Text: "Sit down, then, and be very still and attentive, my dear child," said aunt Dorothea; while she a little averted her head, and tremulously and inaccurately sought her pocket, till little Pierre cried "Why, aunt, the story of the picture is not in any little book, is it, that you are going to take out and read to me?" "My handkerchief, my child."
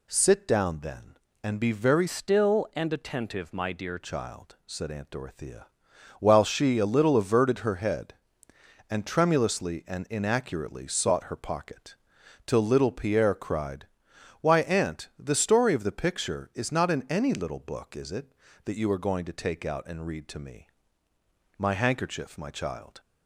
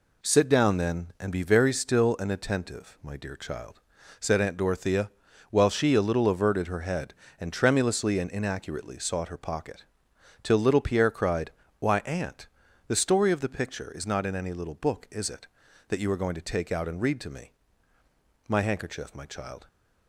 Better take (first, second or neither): second